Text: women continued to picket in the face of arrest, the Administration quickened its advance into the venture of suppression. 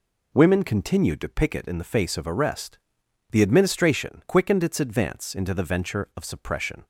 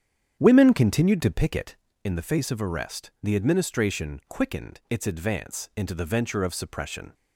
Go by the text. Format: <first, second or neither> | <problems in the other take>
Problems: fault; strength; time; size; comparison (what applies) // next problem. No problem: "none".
first | starts louder than the rest; strong; until 1.9 s; 9 dB